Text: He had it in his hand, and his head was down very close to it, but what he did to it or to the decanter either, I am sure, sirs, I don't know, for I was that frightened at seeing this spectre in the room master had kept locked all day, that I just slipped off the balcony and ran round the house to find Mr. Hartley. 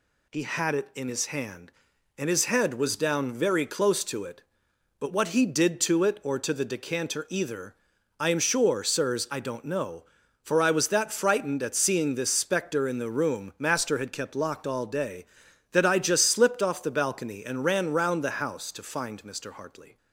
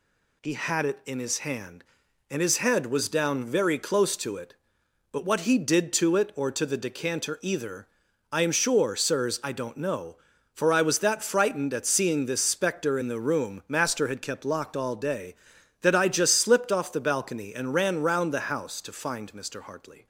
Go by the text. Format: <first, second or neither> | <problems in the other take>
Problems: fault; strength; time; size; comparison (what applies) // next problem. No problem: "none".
neither | none